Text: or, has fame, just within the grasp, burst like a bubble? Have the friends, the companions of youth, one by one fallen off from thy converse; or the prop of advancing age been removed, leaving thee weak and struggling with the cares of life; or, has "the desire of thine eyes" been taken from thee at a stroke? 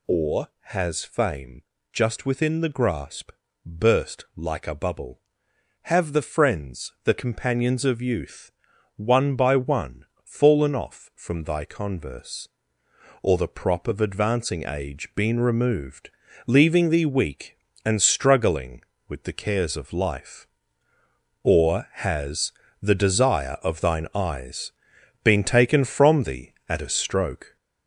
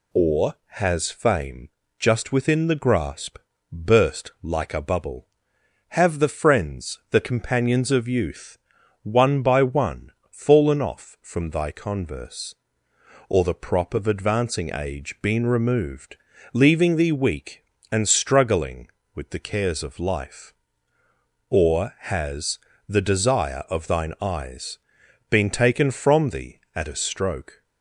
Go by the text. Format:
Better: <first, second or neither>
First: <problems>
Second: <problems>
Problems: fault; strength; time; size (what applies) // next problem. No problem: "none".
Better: second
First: gets louder; noticeable; throughout; 5.5 dB // pauses between "one" and "fallen"; slight; at 10.0 s; 0.20 s long // pauses between "has" and "the"; slight; at 22.5 s; 0.30 s long // pauses between "eyes" and "been"; noticeable; at 24.7 s; 0.50 s long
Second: pauses between "one" and "fallen"; slight; at 10.1 s; 0.20 s long // pauses between "has" and "the"; slight; at 22.5 s; 0.30 s long // pauses between "eyes" and "been"; noticeable; at 24.7 s; 0.50 s long